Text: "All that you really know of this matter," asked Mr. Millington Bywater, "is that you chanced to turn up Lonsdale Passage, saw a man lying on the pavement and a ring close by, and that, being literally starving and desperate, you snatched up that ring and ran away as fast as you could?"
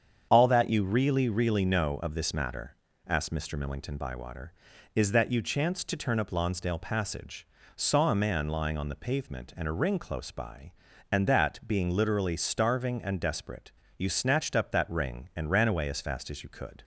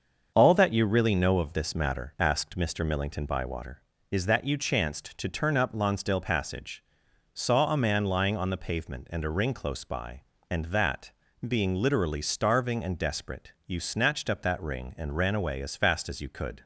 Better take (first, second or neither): second